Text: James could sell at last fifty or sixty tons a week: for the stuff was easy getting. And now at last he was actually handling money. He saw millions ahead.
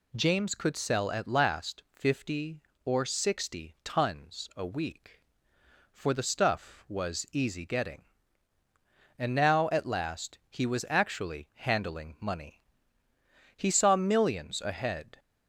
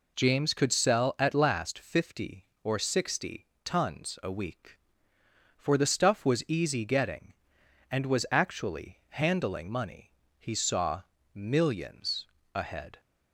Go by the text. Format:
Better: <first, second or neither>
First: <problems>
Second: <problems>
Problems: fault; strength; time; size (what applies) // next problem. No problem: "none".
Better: first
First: none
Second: pauses between "sixty" and "tons"; slight; at 3.4 s; 0.16 s long // skips "now at last he"; at 8.0 s // pauses between "saw" and "millions"; slight; at 11.0 s; 0.32 s long // pauses between "millions" and "ahead"; slight; at 12.2 s; 0.26 s long